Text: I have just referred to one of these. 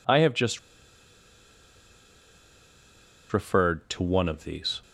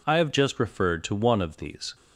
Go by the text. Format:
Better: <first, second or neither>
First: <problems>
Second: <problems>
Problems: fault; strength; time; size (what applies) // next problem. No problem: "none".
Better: second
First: pauses between "just" and "referred"; strong; at 0.5 s; 2.7 s long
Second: none